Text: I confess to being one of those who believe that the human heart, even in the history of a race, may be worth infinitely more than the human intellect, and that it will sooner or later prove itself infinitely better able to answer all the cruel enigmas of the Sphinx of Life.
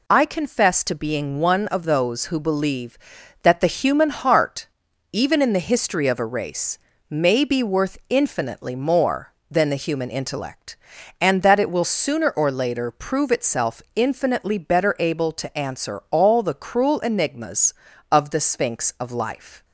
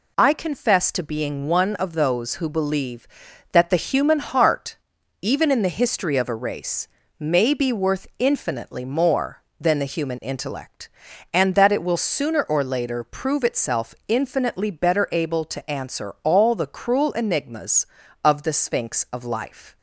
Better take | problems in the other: neither | none

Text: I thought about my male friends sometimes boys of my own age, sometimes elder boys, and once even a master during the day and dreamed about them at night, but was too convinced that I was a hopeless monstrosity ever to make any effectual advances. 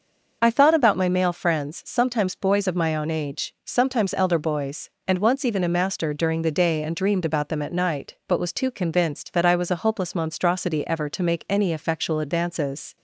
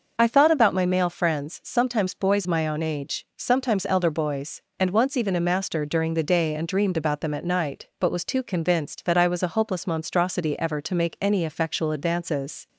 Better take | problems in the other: first | starts louder than the rest; noticeable; until 1.1 s; 6 dB; noticeable in the first // skips "of"; at 2.4 s

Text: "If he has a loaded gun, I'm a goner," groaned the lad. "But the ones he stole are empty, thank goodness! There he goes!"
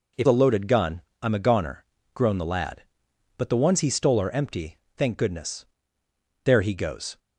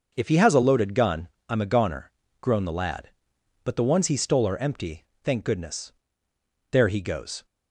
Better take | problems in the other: second | skips "he has"; at 0.2 s

